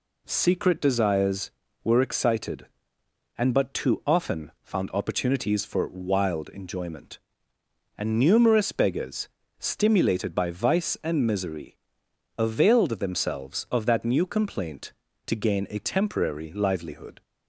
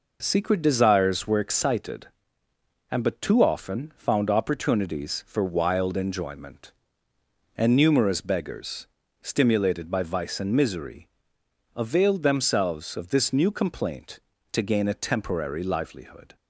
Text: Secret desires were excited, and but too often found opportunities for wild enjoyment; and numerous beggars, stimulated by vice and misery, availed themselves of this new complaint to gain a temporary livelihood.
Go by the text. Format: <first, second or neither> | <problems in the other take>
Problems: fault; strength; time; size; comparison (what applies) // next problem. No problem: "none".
second | says "that" for "this"; at 13.8 s